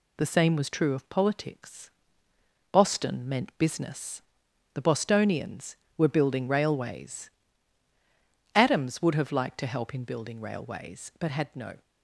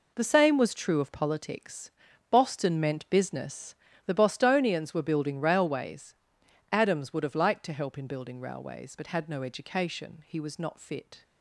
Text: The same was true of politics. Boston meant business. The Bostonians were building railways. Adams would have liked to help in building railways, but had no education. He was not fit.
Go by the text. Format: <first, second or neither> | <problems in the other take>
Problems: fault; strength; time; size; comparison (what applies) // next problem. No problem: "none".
second | stops before "education He was not fit"; at 11.8 s